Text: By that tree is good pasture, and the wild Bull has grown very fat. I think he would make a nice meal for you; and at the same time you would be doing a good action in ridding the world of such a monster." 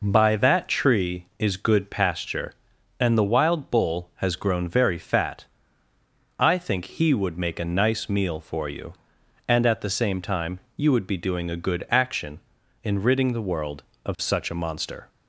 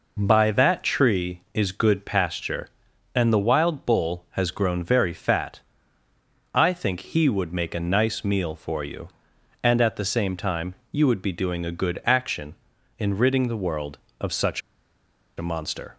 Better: first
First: pauses between "time" and "you"; slight; at 10.5 s; 0.16 s long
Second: pauses between "time" and "you"; slight; at 10.7 s; 0.16 s long // pauses between "such" and "a"; noticeable; at 14.5 s; 0.77 s long

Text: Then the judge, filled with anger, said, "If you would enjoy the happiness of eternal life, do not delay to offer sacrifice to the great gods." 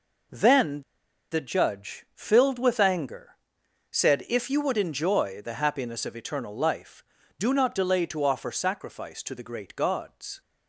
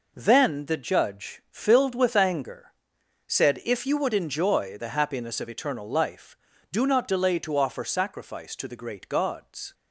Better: second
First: pauses between "Then" and "the"; noticeable; at 0.8 s; 0.49 s long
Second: none

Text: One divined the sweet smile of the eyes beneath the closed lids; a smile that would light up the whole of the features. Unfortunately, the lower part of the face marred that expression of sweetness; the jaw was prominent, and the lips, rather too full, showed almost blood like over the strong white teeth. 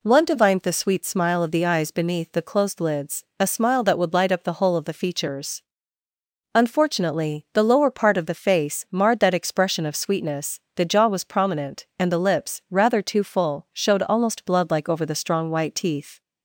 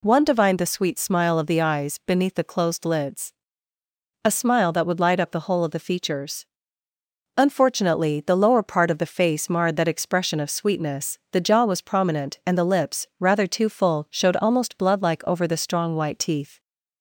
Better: neither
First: none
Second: none

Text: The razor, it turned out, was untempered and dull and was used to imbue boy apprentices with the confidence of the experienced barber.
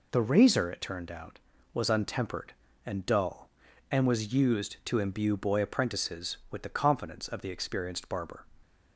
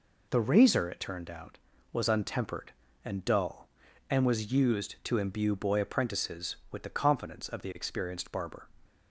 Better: neither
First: none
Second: none

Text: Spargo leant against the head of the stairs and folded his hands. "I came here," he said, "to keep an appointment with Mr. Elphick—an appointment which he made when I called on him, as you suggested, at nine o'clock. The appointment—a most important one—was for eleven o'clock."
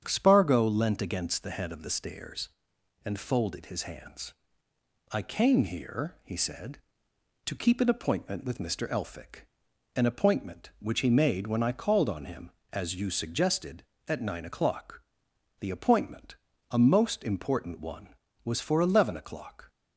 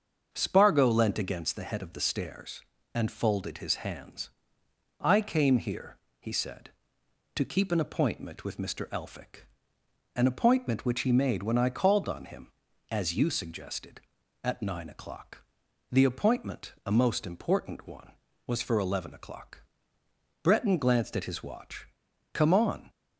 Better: first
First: starts louder than the rest; strong; until 1.1 s; 8 dB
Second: starts louder than the rest; until 1.3 s; 7 dB // goes on to say "Breton glanced at his watch Come on"; strong; from 20.4 s on; 2.4 s long

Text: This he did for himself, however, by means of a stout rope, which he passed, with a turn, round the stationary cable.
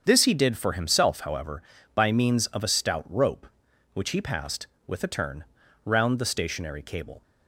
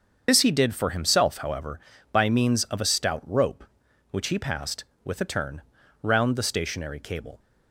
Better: first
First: starts louder than the rest; strong; until 1.0 s; 7 dB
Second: loses the start of "This"; at 0.2 s; 55 ms // starts louder than the rest; until 1.2 s; 7 dB

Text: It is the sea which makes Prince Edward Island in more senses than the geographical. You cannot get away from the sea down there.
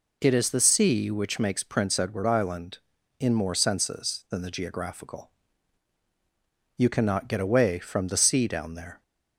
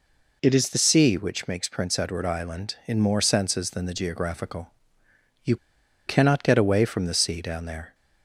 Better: first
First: none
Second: pauses between "You" and "cannot"; noticeable; at 5.5 s; 0.51 s long

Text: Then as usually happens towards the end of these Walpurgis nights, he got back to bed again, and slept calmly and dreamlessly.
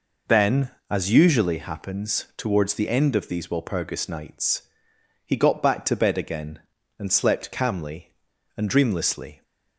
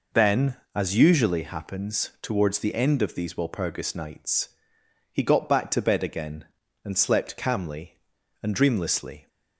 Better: neither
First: none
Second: none

